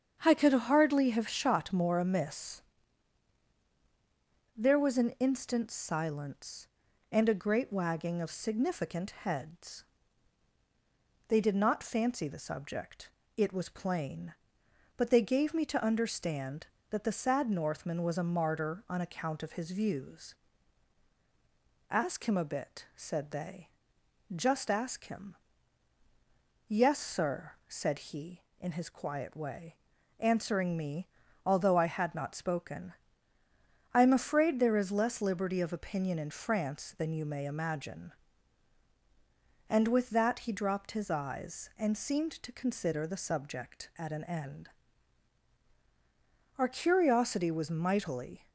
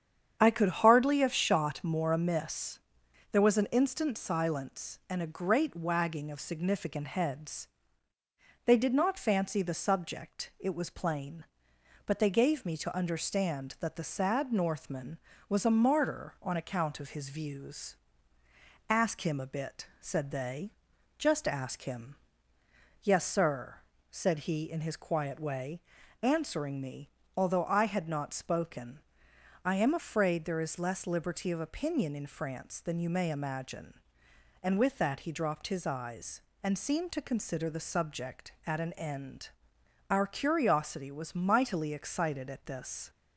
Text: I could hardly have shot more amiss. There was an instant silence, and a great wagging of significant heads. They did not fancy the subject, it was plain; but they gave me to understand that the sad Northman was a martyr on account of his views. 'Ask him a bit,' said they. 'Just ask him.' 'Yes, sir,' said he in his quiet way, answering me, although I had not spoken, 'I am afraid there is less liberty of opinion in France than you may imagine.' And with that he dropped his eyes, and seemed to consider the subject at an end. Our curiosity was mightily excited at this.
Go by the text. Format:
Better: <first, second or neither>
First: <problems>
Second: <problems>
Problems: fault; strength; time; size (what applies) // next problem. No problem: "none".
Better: second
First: starts louder than the rest; strong; until 1.2 s; 7.5 dB // stops before "excited at this"; at 48.4 s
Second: starts louder than the rest; strong; until 1.4 s; 8 dB